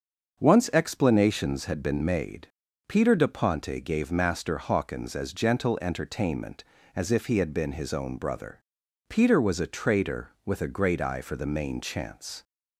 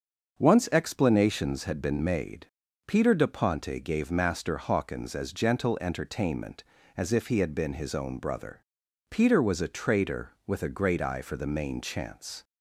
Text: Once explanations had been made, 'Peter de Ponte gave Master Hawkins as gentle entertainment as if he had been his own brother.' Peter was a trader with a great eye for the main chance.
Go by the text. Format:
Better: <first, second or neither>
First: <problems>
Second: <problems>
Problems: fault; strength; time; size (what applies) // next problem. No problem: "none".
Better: neither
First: starts louder than the rest; until 1.4 s; 6.5 dB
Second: starts louder than the rest; until 1.4 s; 6.5 dB